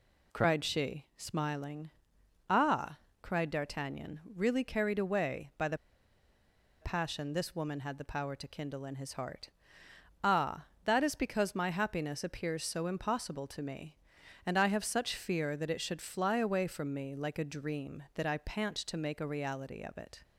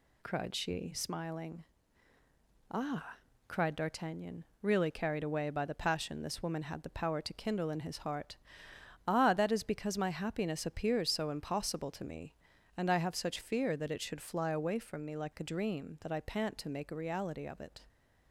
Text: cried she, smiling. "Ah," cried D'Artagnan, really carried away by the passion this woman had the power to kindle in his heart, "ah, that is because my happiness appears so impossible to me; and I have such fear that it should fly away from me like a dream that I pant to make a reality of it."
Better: second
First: pauses between "the" and "passion"; at 5.7 s; 1.0 s long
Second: none

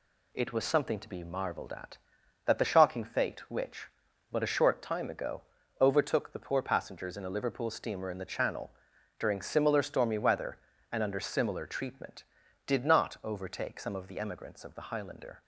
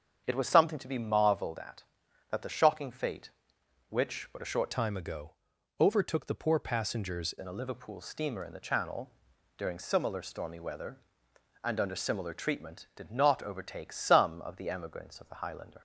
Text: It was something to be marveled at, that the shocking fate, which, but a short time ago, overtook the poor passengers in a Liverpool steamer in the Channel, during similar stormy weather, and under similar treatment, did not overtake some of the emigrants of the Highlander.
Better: first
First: none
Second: starts louder than the rest; strong; until 1.2 s; 7.5 dB // changes voice from "time" to "passengers"; from 4.7 to 7.3 s; 2.6 s long

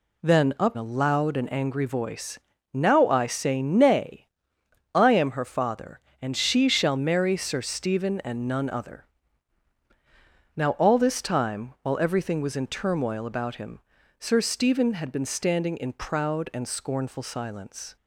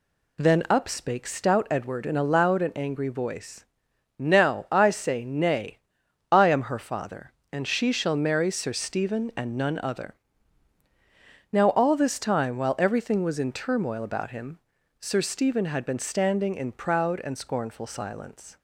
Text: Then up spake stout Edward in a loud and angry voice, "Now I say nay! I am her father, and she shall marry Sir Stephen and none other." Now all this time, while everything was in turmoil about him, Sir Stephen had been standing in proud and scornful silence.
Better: second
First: skips "spake stout Edward in"; at 0.7 s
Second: none

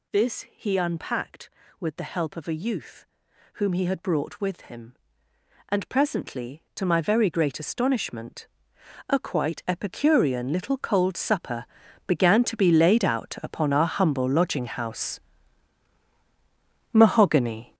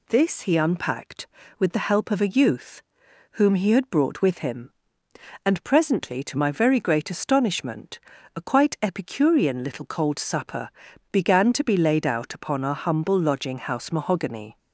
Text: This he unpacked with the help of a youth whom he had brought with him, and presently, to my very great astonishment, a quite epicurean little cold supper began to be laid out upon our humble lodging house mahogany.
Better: second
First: gets louder; strong; throughout; 9 dB // pauses between "youth" and "whom"; noticeable; at 3.0 s; 0.50 s long // pauses between "supper" and "began"; at 11.6 s; 0.40 s long // pauses between "house" and "mahogany"; strong; at 15.2 s; 1.7 s long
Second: pauses between "youth" and "whom"; noticeable; at 2.8 s; 0.50 s long // pauses between "supper" and "began"; at 10.6 s; 0.40 s long

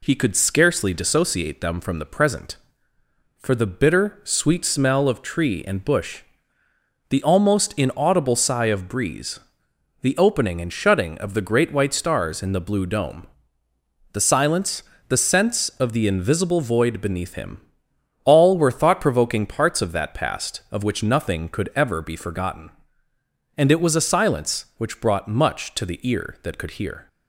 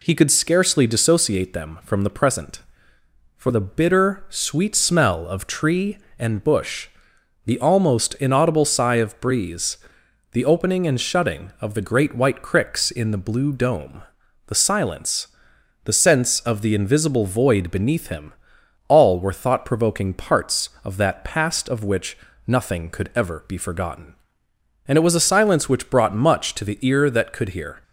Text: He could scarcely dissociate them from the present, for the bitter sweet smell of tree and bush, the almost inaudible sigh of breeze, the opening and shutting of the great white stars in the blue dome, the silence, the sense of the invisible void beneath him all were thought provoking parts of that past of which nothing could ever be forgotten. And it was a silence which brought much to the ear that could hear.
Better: first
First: pauses between "him" and "all"; noticeable; at 17.6 s; 0.64 s long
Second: says "cricks" for "stars"; at 12.4 s // pauses between "him" and "all"; noticeable; at 18.3 s; 0.56 s long // pauses between "which" and "nothing"; slight; at 22.1 s; 0.30 s long

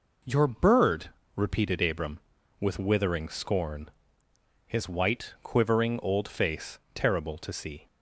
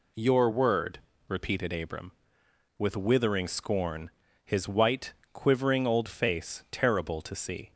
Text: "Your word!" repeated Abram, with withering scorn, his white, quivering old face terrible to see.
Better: second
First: says "bird" for "word"; at 0.4 s // pauses between "face" and "terrible"; slight; at 6.7 s; 0.16 s long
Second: none

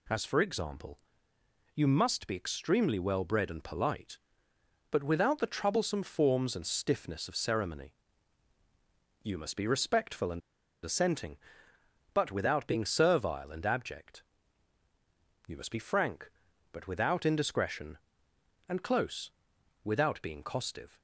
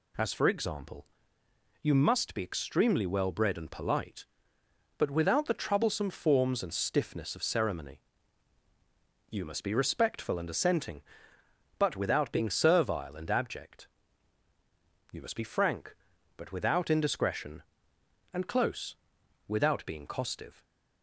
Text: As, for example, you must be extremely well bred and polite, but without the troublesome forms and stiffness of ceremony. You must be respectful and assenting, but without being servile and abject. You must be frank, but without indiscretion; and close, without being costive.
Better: second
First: pauses between "and" and "assenting"; at 10.4 s; 0.43 s long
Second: none

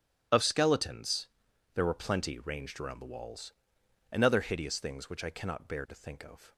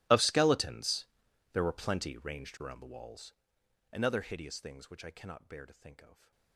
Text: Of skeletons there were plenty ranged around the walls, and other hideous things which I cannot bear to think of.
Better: first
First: starts louder than the rest; strong; until 1.7 s; 10.5 dB // pauses between "skeletons" and "there"; noticeable; at 1.2 s; 0.46 s long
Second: gets quieter; strong; throughout; 24 dB // starts louder than the rest; strong; until 1.5 s; 19 dB // pauses between "skeletons" and "there"; noticeable; at 1.0 s; 0.46 s long

